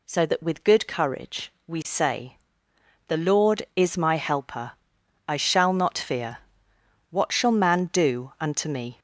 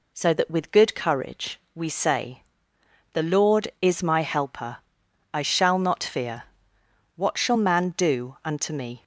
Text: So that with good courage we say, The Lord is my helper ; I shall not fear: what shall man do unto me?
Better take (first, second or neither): second